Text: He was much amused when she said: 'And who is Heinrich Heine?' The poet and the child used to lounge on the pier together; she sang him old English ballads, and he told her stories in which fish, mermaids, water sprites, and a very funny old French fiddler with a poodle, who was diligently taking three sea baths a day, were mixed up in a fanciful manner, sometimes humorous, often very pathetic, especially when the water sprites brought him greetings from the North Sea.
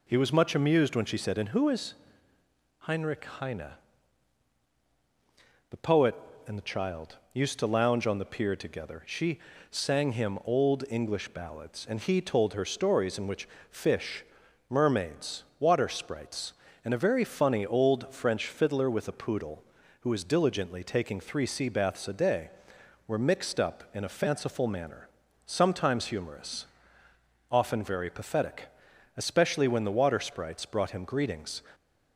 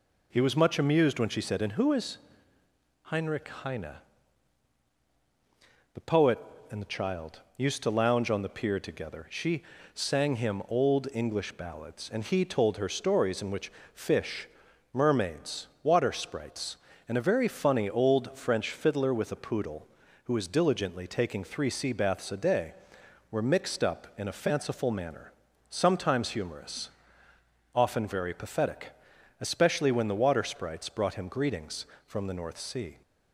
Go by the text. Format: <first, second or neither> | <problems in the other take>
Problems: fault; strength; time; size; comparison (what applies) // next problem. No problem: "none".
second | pauses between "is" and "Heinrich"; noticeable; at 1.9 s; 0.86 s long; noticeable in the second // pauses between "child" and "used"; slight; at 7.1 s; 0.16 s long; slight in the second // pauses between "she" and "sang"; slight; at 9.3 s; 0.32 s long; slight in the second // pauses between "which" and "fish"; slight; at 13.4 s; 0.22 s long; slight in the second // stops before "from the North Sea"; at 31.7 s